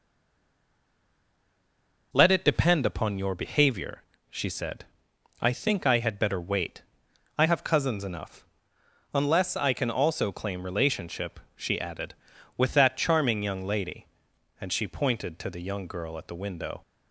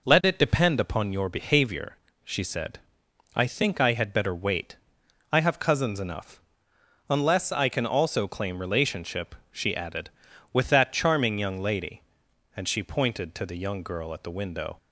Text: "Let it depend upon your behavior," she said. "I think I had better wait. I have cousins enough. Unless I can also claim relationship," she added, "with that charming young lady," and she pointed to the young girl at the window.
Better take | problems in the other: second | stays silent before the first word; until 2.1 s; 2.1 s long

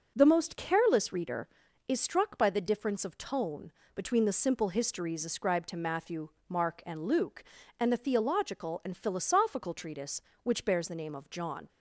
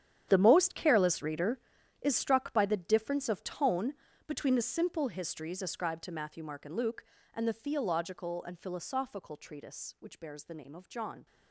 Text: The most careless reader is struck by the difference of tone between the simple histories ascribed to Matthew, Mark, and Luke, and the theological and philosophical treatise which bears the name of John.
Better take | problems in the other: first | gets quieter; strong; throughout; 16 dB // pauses between "tone" and "between"; slight; at 3.9 s; 0.34 s long; slight in the first

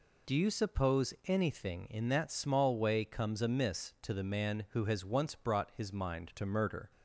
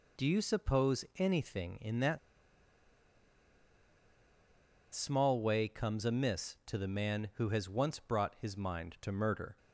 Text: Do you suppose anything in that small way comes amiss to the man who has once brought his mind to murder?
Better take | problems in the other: first | pauses between "that" and "small"; strong; at 2.1 s; 2.7 s long

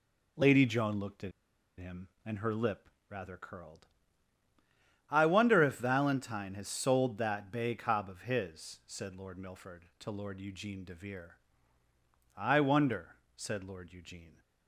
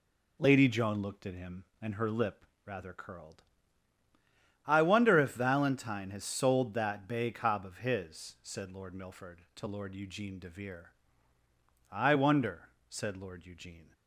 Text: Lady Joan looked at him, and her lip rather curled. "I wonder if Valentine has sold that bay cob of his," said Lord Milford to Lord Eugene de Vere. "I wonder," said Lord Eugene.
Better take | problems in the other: second | pauses between "at" and "him"; noticeable; at 1.3 s; 0.48 s long // pauses between "lip" and "rather"; slight; at 2.8 s; 0.22 s long; slight in the second

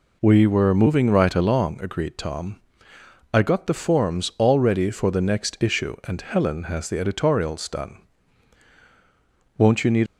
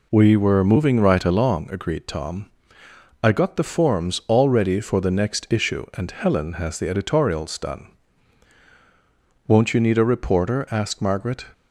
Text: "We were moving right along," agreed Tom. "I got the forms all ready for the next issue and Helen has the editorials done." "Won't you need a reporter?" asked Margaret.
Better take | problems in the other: second | stops before "a reporter asked Margaret"; at 10.0 s

